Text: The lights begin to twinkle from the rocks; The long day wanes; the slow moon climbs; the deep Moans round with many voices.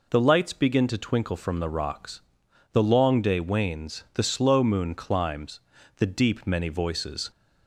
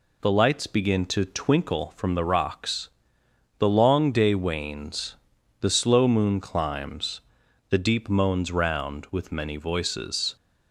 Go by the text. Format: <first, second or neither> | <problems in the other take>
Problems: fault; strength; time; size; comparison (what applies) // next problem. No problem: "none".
second | skips "Moans round with"; at 6.4 s